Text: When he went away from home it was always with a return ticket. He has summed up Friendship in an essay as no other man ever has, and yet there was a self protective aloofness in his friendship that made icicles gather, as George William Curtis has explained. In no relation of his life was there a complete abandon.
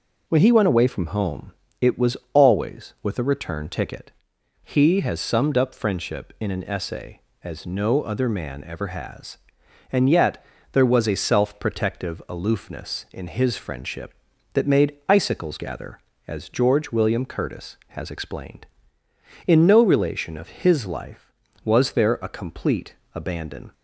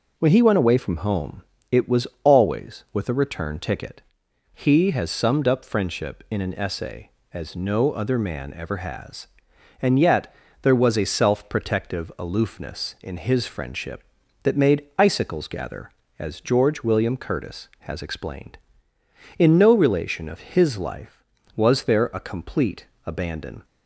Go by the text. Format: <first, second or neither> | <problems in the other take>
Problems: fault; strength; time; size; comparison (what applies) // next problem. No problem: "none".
neither | pauses between "home" and "it"; slight; the same in both // pauses between "was" and "always"; slight; the same in both // pauses between "yet" and "there"; slight; the same in both // pauses between "complete" and "abandon"; slight; the same in both